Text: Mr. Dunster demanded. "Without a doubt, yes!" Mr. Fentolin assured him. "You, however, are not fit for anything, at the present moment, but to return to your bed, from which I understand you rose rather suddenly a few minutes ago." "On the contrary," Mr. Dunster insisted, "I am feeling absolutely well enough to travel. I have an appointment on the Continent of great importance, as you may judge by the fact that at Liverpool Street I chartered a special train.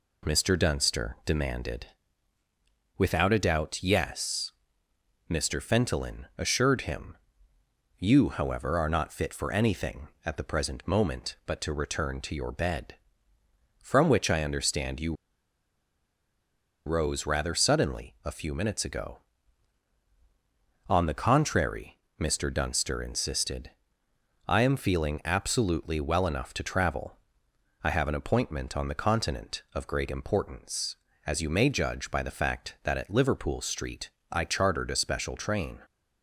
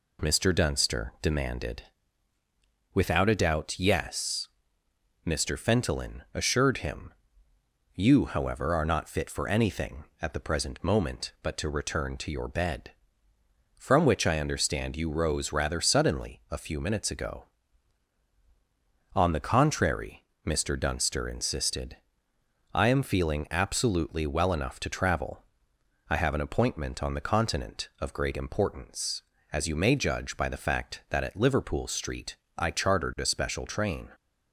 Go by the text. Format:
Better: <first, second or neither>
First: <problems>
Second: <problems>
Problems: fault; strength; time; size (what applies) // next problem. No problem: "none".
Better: second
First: pauses between "you" and "rose"; strong; at 15.1 s; 1.7 s long // pauses between "Street" and "I"; slight; at 34.0 s; 0.20 s long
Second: pauses between "Street" and "I"; slight; at 32.3 s; 0.20 s long